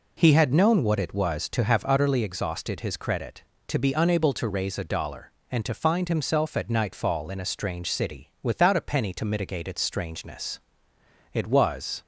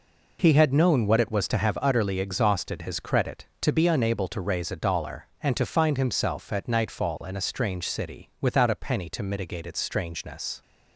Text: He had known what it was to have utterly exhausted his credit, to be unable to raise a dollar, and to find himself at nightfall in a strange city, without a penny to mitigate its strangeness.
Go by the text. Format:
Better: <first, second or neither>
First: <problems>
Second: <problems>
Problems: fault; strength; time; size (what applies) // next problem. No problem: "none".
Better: second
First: goes on to say "It was"; noticeable; from 11.3 s on; 0.68 s long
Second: none